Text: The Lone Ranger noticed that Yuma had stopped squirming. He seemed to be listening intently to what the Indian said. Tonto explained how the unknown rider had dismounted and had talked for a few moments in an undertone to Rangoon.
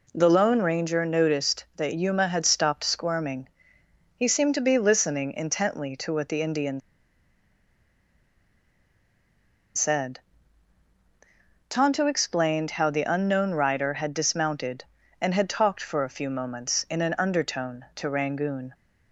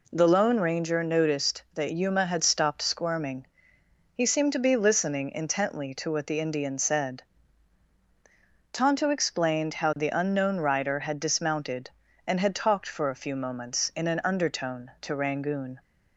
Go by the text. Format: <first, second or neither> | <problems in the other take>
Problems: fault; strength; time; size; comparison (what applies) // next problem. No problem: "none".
second | pauses between "Indian" and "said"; strong; at 6.7 s; 2.9 s long